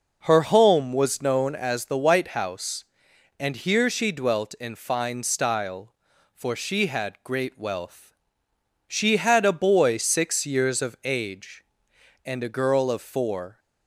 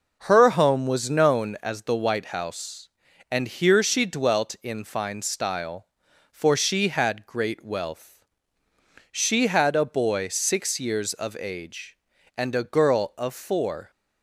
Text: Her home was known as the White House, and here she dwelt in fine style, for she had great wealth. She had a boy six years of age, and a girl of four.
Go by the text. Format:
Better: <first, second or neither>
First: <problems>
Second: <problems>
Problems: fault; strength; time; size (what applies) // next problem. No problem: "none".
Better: neither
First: none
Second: none